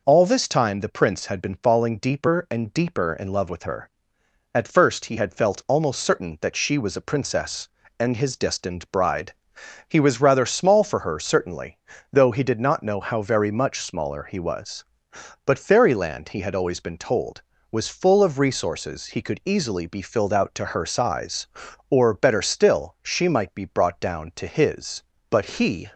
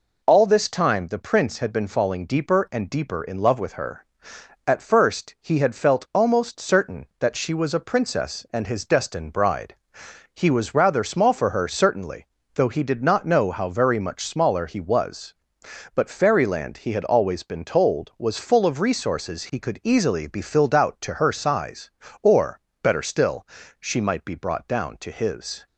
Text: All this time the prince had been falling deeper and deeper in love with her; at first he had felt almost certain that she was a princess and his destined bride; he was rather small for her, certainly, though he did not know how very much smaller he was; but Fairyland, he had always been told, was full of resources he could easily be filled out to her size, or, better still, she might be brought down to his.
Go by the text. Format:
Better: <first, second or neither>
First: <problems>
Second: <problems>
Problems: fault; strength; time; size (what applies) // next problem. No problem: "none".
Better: second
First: goes on to say "But he"; noticeable; from 25.2 s on; 0.62 s long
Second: none